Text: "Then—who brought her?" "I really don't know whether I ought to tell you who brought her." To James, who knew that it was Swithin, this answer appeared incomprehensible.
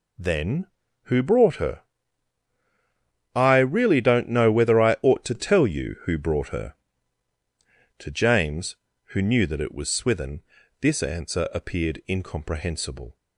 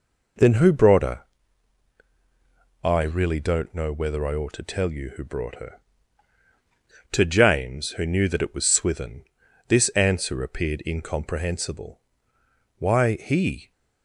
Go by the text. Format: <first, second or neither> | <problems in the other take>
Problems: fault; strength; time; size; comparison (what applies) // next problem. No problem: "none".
first | goes on to say "Why he"; noticeable; from 12.7 s on; 0.94 s long